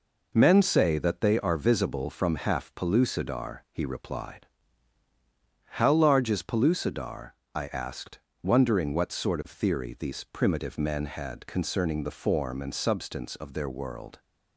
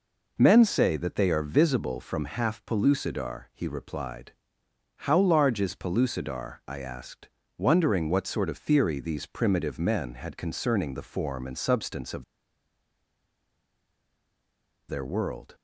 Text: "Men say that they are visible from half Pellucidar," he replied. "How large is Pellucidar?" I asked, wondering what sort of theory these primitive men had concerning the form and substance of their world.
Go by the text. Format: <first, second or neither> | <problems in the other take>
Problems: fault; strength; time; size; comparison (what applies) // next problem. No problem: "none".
first | pauses between "of" and "their"; strong; at 12.2 s; 2.6 s long